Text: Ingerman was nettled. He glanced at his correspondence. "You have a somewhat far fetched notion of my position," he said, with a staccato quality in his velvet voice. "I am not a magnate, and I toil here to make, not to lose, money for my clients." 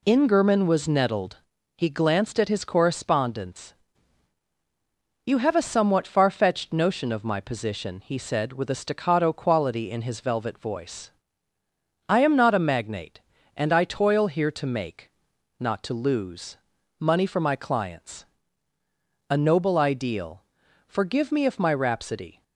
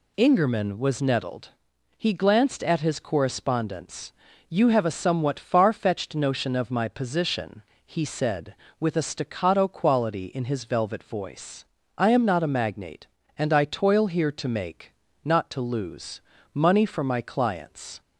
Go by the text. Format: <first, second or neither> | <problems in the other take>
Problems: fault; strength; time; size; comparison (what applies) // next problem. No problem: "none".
second | goes on to say "A noble ideal Forgive me if my rhapsody"; strong; from 19.3 s on; 3.1 s long